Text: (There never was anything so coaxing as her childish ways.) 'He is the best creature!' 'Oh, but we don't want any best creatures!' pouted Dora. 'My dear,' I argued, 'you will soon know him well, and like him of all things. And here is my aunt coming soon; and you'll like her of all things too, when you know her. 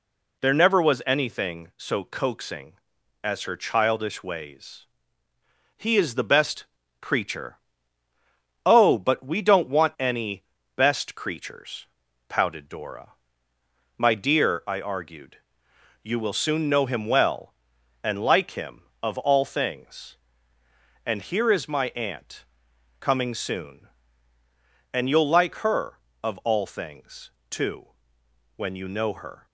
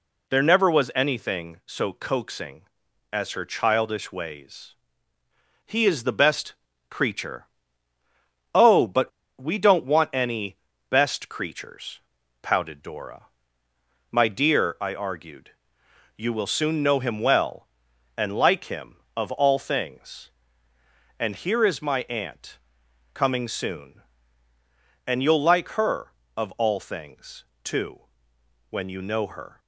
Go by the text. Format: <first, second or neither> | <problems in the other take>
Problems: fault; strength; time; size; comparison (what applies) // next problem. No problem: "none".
first | pauses between "best" and "creature"; slight; at 6.5 s; 0.36 s long; slight in the first // pauses between "but" and "we"; slight; at 9.0 s; 0.31 s long // pauses between "any" and "best"; slight; at 10.5 s; 0.32 s long; slight in the first // pauses between "aunt" and "coming"; noticeable; at 22.5 s; 0.54 s long; noticeable in the first // pauses between "things" and "too"; slight; at 27.4 s; 0.22 s long; slight in the first